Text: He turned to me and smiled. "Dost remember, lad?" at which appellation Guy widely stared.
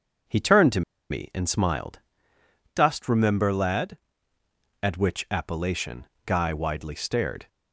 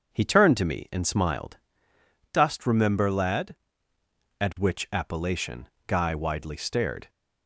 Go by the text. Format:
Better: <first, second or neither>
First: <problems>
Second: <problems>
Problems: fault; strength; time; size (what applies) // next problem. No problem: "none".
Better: second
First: pauses between "to" and "me"; slight; at 0.8 s; 0.28 s long // pauses between "appellation" and "Guy"; slight; at 6.0 s; 0.22 s long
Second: pauses between "appellation" and "Guy"; slight; at 5.6 s; 0.22 s long